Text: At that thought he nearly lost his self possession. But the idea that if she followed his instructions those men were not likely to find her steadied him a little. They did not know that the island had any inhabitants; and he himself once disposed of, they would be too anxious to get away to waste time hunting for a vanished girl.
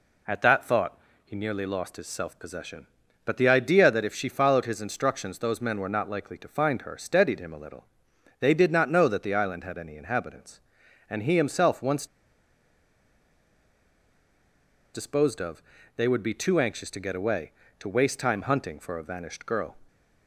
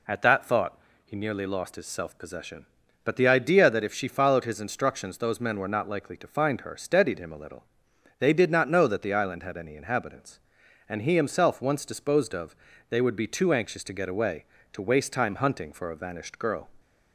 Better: second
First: pauses between "thought" and "he"; slight; at 0.9 s; 0.28 s long // pauses between "once" and "disposed"; strong; at 12.0 s; 2.8 s long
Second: pauses between "thought" and "he"; slight; at 0.7 s; 0.28 s long

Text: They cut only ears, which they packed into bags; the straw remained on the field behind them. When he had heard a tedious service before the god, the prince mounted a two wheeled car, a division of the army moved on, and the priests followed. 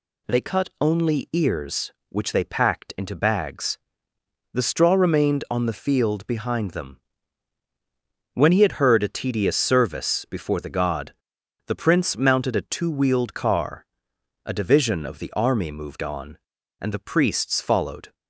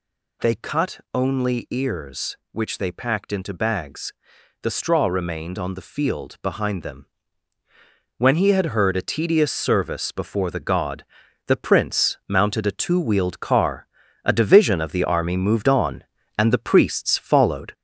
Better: first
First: none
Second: gets louder; noticeable; throughout; 4.5 dB

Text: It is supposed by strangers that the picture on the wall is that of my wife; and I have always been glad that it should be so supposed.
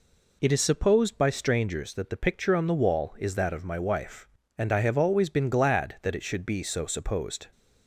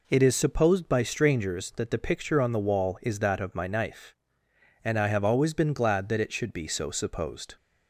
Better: first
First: none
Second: says "knife" for "wife"; at 3.6 s

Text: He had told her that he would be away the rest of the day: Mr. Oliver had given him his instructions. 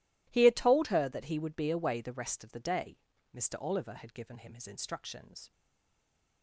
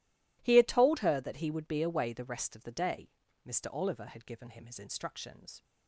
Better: second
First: stays silent after the last word; slight; from 5.5 s on; 0.9 s long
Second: none

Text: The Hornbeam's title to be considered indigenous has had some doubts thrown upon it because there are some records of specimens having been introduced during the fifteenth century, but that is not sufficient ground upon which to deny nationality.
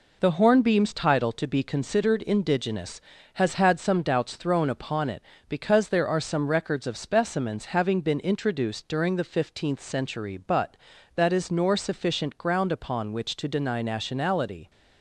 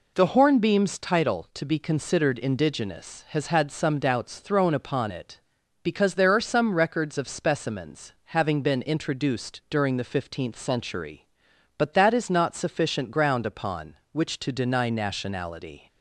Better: second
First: says "nor" for "not"; at 11.4 s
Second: none

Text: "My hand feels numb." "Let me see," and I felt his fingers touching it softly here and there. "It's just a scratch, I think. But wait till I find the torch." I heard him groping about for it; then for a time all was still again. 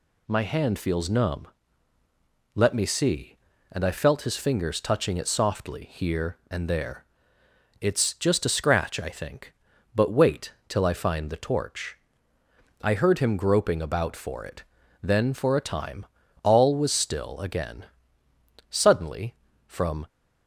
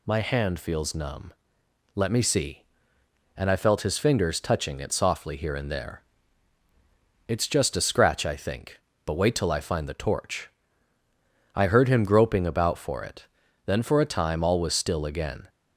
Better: second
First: pauses between "wait" and "till"; slight; at 10.5 s; 0.16 s long // pauses between "time" and "all"; slight; at 16.0 s; 0.36 s long // goes on to say "Suddenly from"; from 18.6 s on; 1.3 s long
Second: none

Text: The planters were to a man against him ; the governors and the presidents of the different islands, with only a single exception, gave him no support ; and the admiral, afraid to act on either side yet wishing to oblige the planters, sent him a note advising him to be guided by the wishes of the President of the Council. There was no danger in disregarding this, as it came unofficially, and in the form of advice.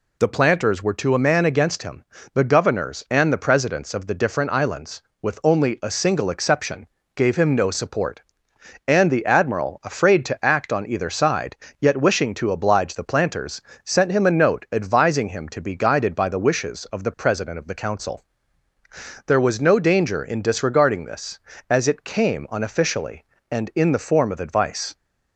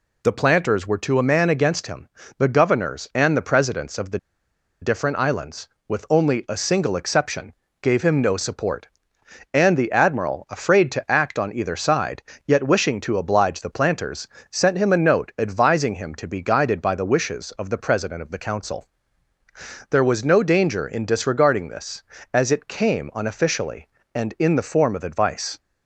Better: first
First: pauses between "side" and "yet"; slight; at 11.5 s; 0.24 s long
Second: pauses between "the" and "different"; noticeable; at 4.1 s; 0.62 s long // pauses between "side" and "yet"; slight; at 12.2 s; 0.24 s long

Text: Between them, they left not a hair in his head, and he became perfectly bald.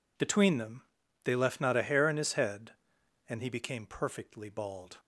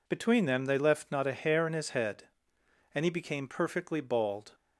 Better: neither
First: none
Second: none

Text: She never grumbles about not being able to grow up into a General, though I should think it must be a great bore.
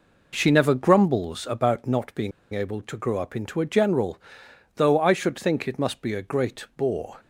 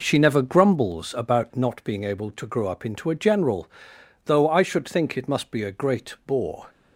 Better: second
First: pauses between "being" and "able"; slight; at 2.3 s; 0.22 s long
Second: none

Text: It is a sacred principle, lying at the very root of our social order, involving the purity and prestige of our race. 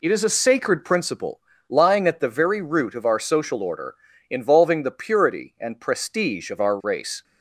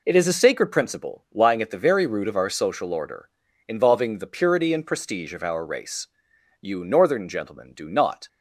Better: first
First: none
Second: goes on to say "You Northern gentlemen do not"; strong; from 6.5 s on; 1.6 s long

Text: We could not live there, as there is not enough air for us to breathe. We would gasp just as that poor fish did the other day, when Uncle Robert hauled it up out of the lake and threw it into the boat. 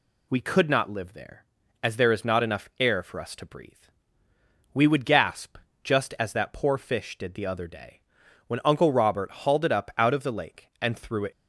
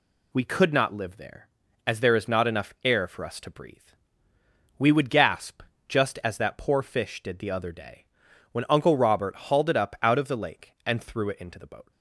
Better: second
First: pauses between "gasp" and "just"; slight; at 5.5 s; 0.28 s long // stops before "into the boat"; at 11.3 s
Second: pauses between "gasp" and "just"; slight; at 5.6 s; 0.28 s long

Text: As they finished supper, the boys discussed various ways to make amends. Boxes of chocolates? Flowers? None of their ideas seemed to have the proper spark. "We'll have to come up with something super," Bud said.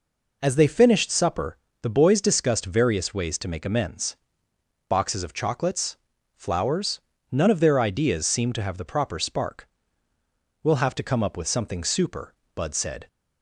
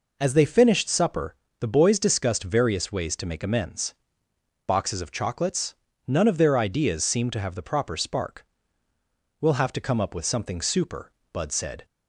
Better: first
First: none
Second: skips "Flowers"; at 5.8 s

